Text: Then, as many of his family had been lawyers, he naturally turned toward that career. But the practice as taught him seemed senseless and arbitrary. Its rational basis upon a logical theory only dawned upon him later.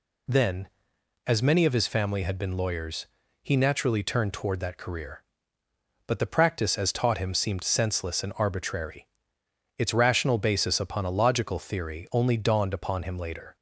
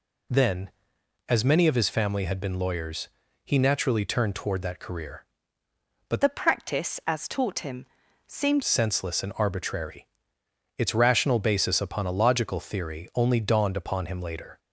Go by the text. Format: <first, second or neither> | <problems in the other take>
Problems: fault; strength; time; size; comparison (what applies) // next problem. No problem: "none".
first | changes voice from "the" to "seemed"; from 6.2 to 8.6 s; 2.4 s long // pauses between "him" and "seemed"; at 7.8 s; 0.40 s long